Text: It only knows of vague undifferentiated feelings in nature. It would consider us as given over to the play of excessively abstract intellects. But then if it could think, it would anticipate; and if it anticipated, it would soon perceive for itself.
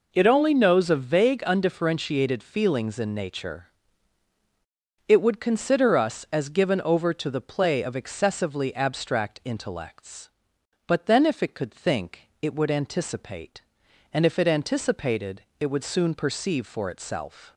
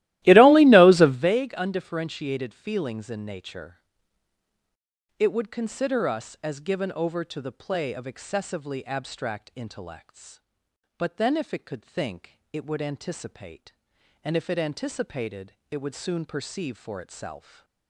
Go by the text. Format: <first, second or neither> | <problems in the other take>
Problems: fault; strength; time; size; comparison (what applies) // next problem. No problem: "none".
first | starts louder than the rest; strong; until 1.4 s; 16 dB // stays silent after the last word; slight; from 17.3 s on; 0.5 s long